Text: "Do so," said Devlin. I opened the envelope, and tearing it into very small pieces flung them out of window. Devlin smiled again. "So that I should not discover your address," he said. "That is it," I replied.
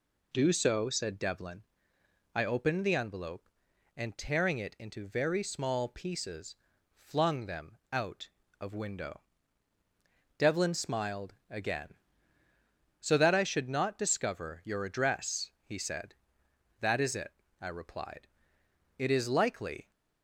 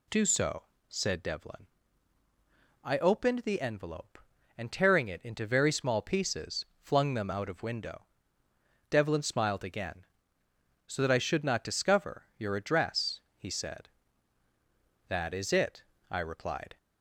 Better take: second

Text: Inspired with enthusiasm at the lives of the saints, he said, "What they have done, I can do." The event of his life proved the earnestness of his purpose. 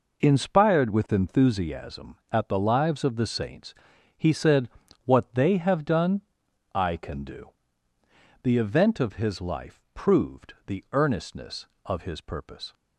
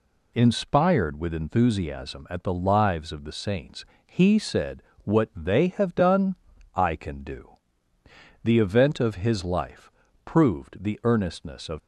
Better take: first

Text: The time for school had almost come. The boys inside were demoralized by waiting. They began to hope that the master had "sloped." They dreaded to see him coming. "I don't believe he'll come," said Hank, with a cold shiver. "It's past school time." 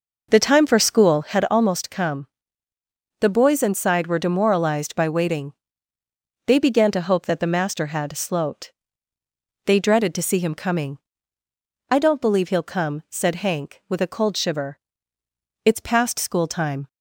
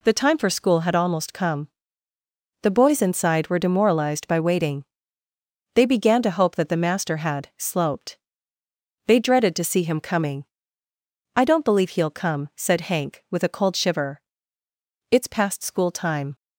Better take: second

